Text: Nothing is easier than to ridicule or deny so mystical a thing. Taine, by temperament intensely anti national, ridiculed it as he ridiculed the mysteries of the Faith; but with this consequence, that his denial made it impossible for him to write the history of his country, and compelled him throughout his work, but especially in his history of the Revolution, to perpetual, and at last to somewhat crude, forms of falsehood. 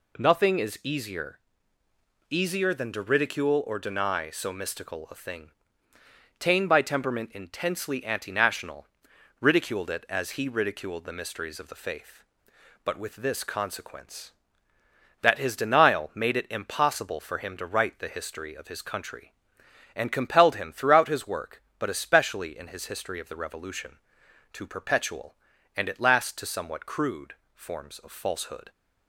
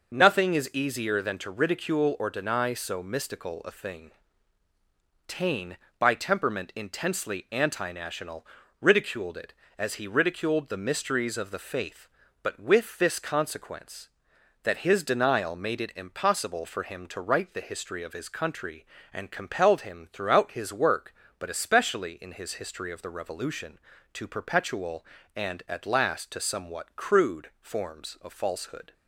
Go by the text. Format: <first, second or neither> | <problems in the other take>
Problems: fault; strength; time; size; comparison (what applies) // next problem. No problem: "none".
second | says "easier" twice; at 2.2 s